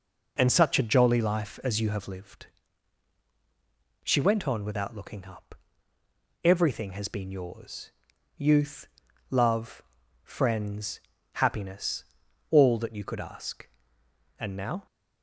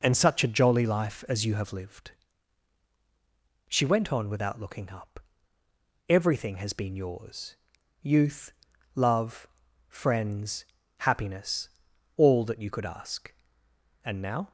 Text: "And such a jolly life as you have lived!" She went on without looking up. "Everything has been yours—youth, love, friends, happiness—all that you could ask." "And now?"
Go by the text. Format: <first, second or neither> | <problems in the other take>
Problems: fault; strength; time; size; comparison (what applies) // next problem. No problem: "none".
neither | none